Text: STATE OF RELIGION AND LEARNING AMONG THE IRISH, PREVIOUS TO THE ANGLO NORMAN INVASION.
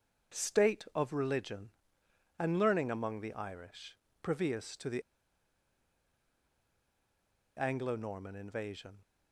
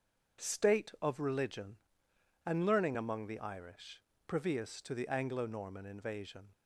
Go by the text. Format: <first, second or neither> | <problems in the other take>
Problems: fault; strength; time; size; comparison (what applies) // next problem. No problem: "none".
second | starts louder than the rest; until 1.4 s; 7 dB; also in the second // pauses between "THE" and "ANGLO"; strong; at 5.0 s; 2.5 s long